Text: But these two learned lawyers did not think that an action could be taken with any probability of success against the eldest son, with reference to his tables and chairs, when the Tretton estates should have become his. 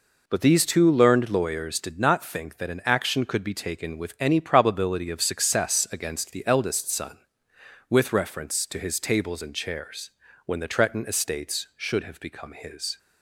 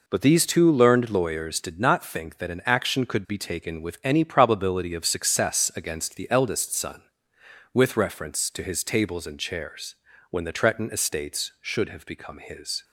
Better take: neither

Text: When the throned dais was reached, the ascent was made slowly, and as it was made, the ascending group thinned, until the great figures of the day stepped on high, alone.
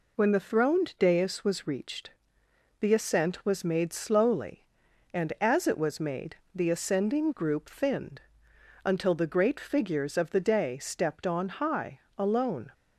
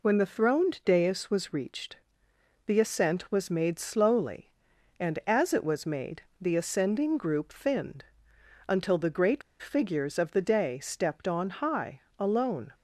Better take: first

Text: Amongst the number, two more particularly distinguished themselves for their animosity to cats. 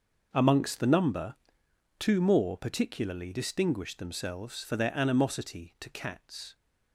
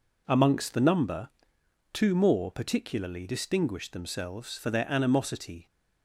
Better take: first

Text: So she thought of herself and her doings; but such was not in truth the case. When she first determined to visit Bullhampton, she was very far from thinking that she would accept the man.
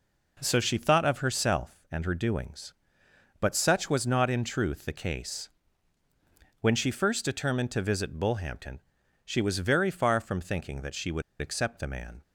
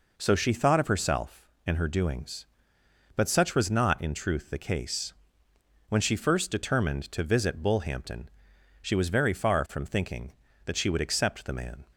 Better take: second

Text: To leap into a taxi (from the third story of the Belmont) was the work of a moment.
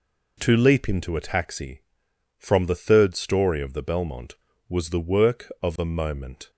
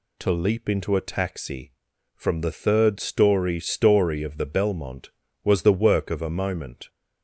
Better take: first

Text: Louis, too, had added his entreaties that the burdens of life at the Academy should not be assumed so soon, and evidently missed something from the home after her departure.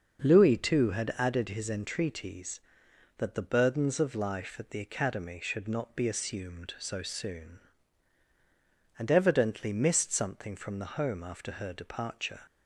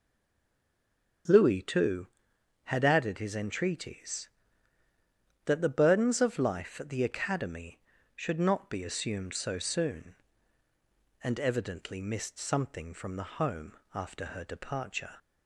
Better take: first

